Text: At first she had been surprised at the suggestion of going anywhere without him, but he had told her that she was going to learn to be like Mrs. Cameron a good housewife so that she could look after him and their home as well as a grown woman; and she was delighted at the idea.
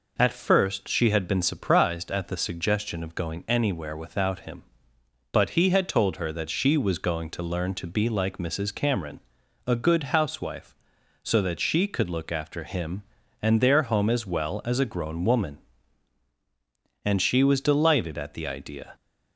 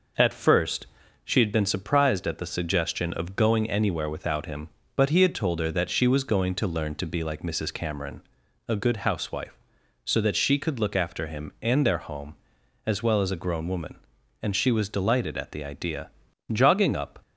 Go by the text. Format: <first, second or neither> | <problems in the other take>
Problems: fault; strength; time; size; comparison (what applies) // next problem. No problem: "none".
first | pauses between "first" and "she"; at 0.8 s; 0.38 s long // pauses between "Cameron" and "a"; noticeable; at 8.2 s; 0.46 s long; noticeable in the first // goes on to say "Jogging up"; noticeable; from 16.4 s on; 0.72 s long